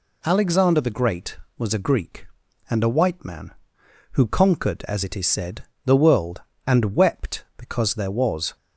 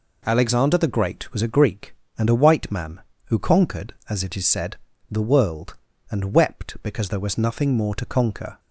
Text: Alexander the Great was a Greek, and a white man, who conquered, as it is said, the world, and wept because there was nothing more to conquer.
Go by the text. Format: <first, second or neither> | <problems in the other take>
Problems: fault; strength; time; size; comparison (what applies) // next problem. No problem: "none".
second | stops before "nothing more to conquer"; at 8.5 s